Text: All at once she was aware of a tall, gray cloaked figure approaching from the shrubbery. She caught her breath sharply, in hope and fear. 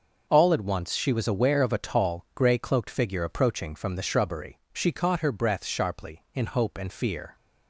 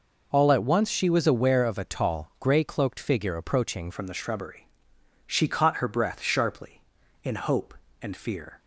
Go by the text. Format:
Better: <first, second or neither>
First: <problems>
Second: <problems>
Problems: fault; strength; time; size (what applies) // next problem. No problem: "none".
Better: first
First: none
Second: changes voice at "from"; from 3.9 s on; 4.6 s long